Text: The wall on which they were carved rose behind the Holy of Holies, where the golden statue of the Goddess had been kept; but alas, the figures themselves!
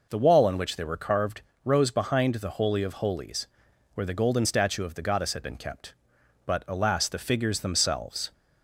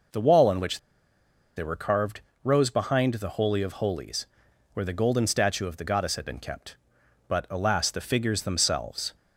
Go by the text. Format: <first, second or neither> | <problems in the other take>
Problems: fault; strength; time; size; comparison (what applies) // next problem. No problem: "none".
first | pauses between "which" and "they"; noticeable; at 0.7 s; 0.77 s long // pauses between "carved" and "rose"; slight; at 2.2 s; 0.22 s long; slight in the first